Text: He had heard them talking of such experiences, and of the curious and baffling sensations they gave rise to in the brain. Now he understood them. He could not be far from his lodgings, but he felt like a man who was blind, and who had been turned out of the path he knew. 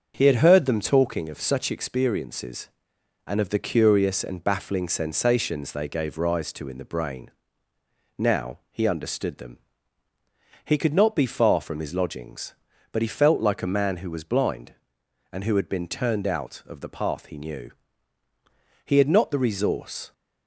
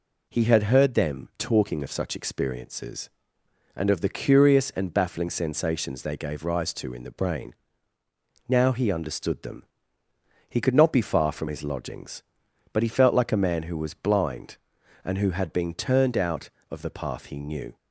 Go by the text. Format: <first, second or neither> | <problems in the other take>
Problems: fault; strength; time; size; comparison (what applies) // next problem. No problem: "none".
second | starts louder than the rest; until 1.1 s; 6.5 dB // goes on to say "He had not the resource"; noticeable; from 18.8 s on; 1.2 s long